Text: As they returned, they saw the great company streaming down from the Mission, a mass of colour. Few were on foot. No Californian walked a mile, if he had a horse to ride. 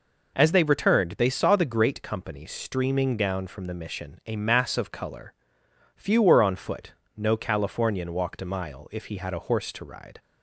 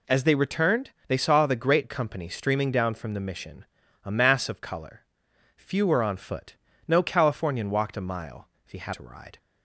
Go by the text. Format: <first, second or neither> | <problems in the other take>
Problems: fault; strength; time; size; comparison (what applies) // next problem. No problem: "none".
first | skips "a horse"; at 8.9 s